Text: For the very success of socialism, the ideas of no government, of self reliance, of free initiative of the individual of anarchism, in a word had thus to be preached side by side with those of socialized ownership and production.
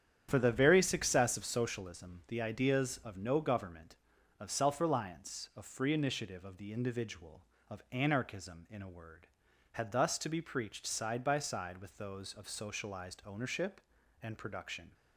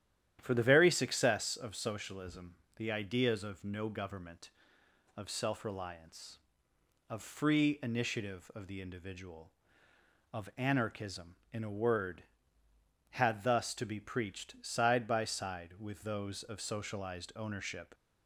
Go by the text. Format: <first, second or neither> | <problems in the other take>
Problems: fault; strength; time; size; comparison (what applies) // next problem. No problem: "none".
first | starts louder than the rest; strong; until 1.4 s; 10.5 dB; strong in the first // stops before "and production"; at 17.9 s